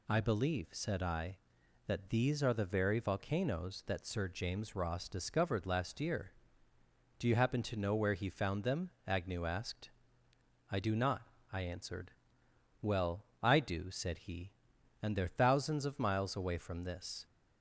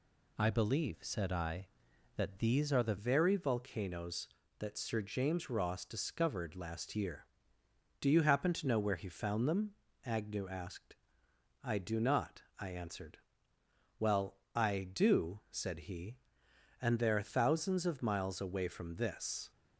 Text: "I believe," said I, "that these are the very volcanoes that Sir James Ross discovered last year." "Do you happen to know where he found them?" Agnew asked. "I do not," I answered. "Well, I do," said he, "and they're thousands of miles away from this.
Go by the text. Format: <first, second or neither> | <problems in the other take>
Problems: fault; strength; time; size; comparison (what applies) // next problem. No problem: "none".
first | changes voice at "very"; from 2.9 s on; 16.6 s long